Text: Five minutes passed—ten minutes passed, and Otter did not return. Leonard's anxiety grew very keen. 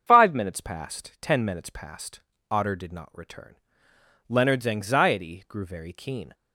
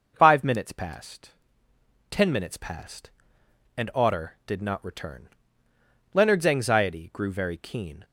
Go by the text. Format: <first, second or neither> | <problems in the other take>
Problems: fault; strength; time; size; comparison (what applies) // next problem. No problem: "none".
second | starts louder than the rest; until 1.0 s; 7 dB // skips "and"; at 2.3 s